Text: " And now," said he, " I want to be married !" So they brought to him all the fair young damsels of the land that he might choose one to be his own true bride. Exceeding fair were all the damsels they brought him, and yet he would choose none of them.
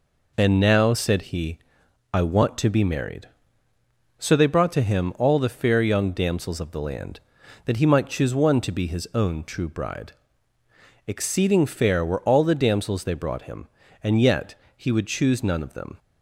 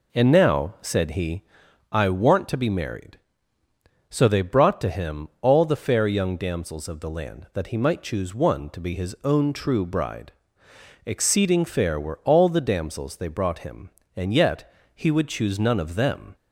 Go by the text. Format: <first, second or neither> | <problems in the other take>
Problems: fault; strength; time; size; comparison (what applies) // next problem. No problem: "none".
neither | pauses between "yet" and "he"; slight; the same in both